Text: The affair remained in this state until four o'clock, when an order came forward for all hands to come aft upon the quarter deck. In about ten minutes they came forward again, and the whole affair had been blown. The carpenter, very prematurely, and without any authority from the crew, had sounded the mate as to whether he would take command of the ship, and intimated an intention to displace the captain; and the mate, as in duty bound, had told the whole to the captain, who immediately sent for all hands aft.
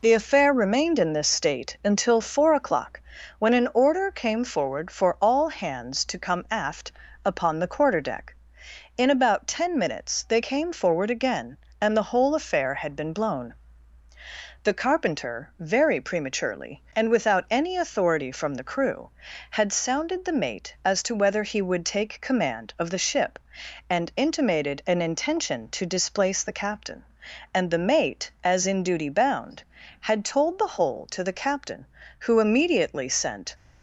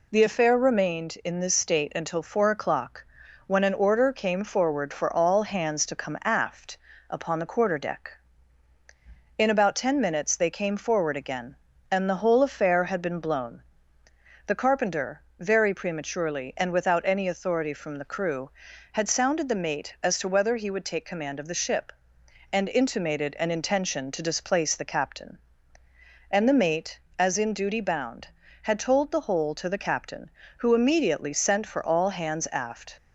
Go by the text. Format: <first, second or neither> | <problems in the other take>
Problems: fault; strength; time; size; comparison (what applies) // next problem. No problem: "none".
second | pauses between "aft" and "upon"; slight; at 6.9 s; 0.34 s long; slight in the second // stops before "for all hands aft"; at 33.5 s